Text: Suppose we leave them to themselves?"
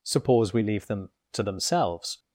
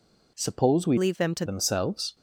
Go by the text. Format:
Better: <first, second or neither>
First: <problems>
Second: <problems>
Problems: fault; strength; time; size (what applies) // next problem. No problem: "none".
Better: first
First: none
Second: changes voice from "leave" to "to"; from 0.9 to 1.4 s; 0.5 s long